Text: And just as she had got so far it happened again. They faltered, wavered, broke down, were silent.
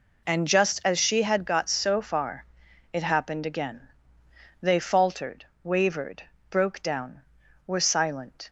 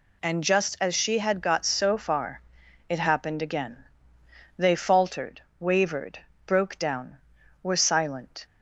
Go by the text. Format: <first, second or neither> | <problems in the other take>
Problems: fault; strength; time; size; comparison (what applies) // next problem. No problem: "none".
second | starts louder than the rest; until 1.5 s; 3.5 dB // pauses between "far" and "it"; noticeable; at 2.4 s; 0.48 s long; noticeable in the second